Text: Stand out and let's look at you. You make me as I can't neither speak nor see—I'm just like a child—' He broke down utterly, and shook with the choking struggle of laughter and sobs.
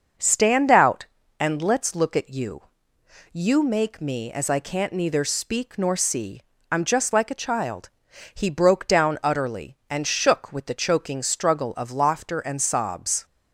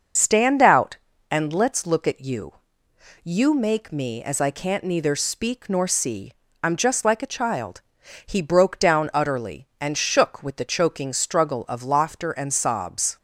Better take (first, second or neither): first